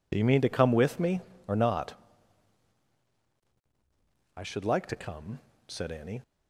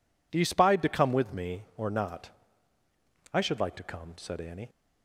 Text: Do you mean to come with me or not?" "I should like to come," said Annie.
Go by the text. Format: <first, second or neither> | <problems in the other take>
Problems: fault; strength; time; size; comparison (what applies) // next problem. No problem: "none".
first | says "spied" for "mean"; at 0.4 s